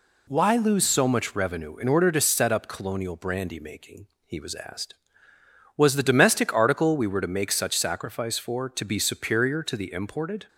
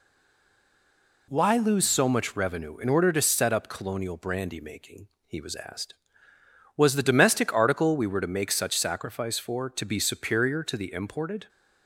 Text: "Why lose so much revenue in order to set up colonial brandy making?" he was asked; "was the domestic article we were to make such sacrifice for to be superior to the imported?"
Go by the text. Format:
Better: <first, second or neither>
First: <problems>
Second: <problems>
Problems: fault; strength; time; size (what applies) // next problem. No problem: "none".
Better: first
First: none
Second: stays silent before the first word; noticeable; until 1.2 s; 1.2 s long